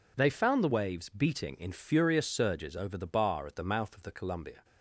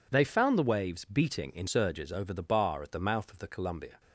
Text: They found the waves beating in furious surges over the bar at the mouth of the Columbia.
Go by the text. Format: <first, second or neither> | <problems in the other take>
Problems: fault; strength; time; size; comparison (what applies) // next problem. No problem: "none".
first | skips "furious"; at 1.6 s